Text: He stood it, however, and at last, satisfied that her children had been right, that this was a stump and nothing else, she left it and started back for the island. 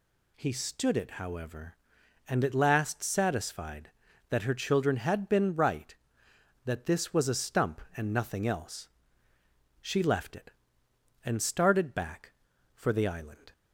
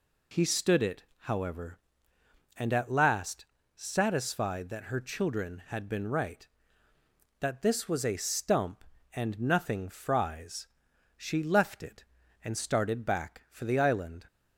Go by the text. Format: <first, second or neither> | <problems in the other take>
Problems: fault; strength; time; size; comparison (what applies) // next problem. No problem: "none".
first | says "fries" for "else"; at 9.8 s